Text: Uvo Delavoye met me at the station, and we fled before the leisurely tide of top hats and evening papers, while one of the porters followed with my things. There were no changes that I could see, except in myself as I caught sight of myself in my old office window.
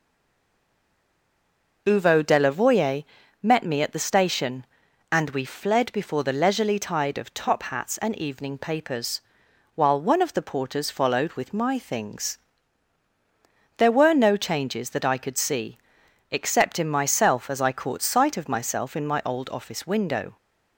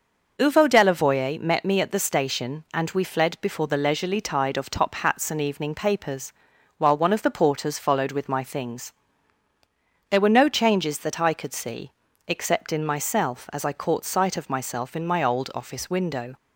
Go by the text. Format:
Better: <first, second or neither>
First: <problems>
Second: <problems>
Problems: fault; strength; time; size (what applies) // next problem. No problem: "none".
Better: second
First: stays silent before the first word; noticeable; until 1.8 s; 1.8 s long // pauses between "Delavoye" and "met"; at 3.0 s; 0.38 s long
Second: none